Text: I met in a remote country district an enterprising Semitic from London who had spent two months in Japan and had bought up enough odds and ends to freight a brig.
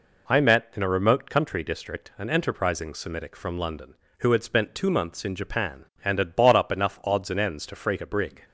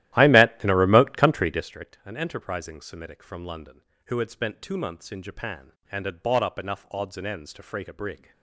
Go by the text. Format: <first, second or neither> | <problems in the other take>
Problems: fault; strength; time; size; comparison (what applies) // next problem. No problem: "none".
first | starts louder than the rest; strong; until 1.8 s; 14 dB